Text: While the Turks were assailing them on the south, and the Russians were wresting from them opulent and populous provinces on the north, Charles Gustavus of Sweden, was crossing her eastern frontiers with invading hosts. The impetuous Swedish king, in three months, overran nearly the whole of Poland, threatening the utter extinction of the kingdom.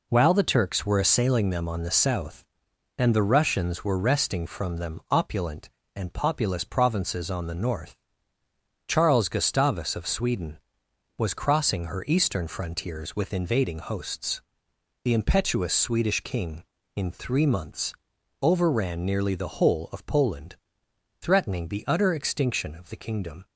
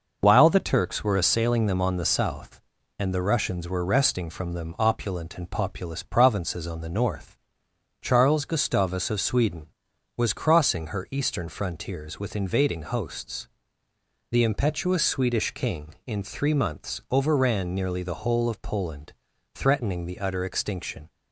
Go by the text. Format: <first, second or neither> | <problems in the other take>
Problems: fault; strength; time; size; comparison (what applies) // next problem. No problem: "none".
first | stops before "of the kingdom"; at 21.0 s